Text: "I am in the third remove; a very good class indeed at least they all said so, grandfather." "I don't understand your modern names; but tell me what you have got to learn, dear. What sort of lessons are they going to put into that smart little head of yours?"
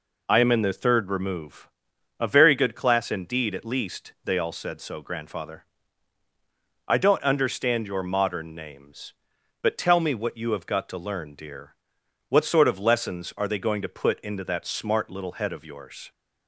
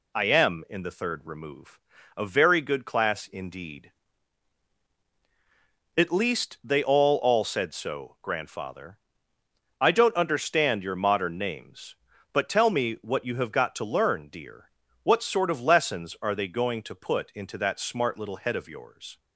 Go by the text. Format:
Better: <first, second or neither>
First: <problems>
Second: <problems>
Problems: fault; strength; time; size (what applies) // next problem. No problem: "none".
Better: first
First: none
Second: says "all" twice; at 7.1 s